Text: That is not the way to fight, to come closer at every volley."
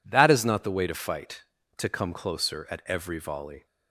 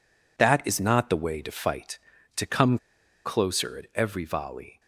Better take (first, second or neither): first